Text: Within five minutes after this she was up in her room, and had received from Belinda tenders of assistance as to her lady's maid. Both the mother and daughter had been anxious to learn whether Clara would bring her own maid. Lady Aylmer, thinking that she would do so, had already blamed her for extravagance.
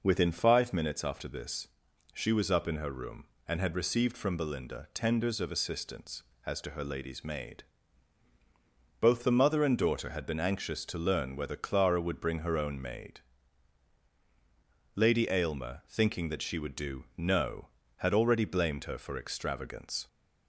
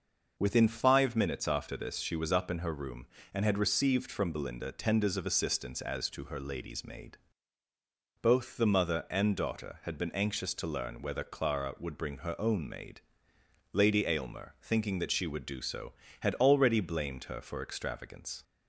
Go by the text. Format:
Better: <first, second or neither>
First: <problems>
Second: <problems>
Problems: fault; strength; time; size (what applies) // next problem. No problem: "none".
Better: second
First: pauses between "this" and "she"; noticeable; at 1.6 s; 0.46 s long // says "no" for "so"; at 17.1 s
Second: none